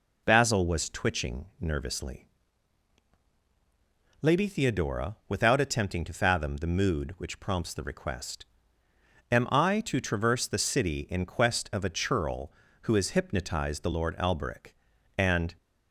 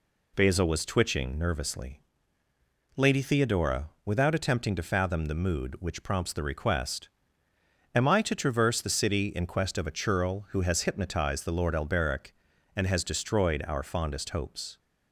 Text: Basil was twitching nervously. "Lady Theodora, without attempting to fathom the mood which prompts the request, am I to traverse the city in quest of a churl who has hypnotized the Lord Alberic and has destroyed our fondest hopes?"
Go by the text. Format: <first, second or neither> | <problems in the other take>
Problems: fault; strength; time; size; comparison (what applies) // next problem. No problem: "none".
second | stops before "has destroyed our fondest hopes"; at 15.5 s